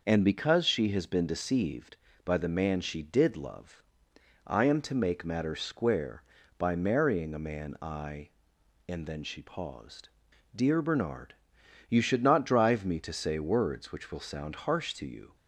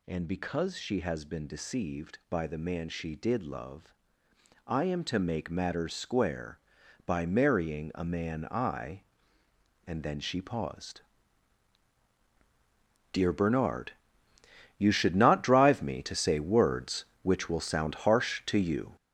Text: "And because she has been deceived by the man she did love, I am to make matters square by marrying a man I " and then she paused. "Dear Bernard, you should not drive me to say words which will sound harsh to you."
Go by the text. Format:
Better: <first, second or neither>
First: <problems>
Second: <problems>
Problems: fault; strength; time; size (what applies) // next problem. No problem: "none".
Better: first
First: none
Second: gets louder; throughout; 7 dB